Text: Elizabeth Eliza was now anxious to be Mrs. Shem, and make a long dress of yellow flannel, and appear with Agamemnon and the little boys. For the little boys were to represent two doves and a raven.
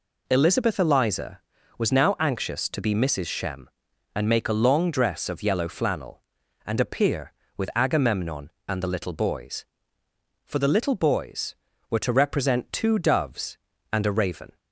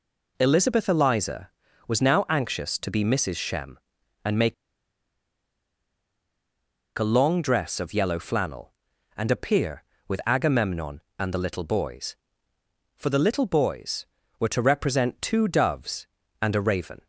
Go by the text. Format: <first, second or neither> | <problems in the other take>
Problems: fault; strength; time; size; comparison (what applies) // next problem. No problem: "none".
first | pauses between "make" and "a"; strong; at 4.5 s; 2.4 s long